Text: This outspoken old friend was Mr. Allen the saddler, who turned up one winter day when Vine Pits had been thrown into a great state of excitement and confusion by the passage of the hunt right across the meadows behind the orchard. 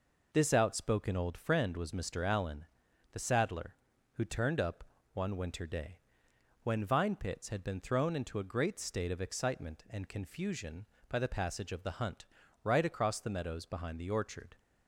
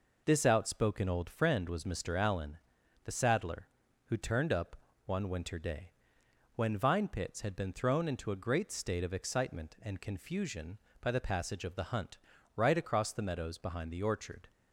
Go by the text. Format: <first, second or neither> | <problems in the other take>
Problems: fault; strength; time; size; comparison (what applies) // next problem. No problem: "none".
neither | pauses between "Allen" and "the"; noticeable; the same in both // pauses between "up" and "one"; slight; the same in both // pauses between "day" and "when"; noticeable; the same in both // pauses between "hunt" and "right"; slight; the same in both